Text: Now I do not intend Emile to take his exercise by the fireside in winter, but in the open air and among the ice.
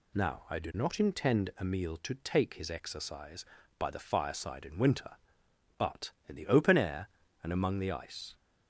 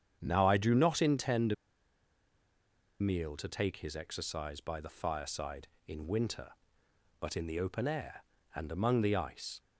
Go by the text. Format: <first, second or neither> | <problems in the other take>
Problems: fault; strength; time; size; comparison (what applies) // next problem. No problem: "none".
first | starts louder than the rest; strong; until 1.2 s; 8 dB // pauses between "intend" and "Emile"; strong; at 1.5 s; 1.4 s long